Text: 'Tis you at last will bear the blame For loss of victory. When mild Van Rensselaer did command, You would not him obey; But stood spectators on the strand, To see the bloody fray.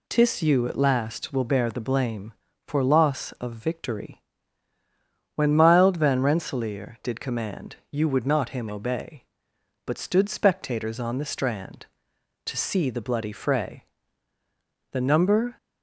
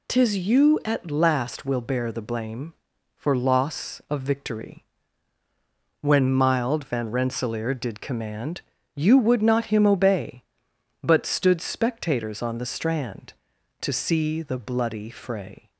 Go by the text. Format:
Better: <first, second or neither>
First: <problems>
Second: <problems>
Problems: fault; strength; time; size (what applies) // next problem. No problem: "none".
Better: second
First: goes on to say "The number"; noticeable; from 14.9 s on; 0.64 s long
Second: none